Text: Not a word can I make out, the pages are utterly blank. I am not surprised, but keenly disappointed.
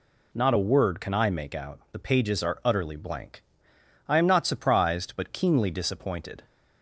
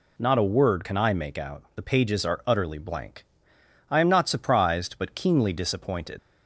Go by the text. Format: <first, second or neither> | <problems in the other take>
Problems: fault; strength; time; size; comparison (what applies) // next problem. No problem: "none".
first | leaves "disappointed" unfinished; at 6.1 s; 85 ms